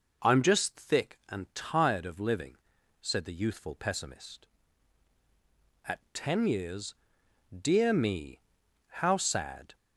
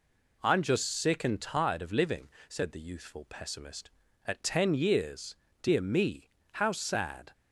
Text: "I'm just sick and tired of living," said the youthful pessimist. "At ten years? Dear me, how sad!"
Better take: second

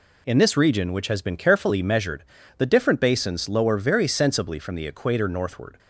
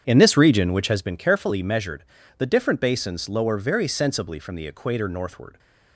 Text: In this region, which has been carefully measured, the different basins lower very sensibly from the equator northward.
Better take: first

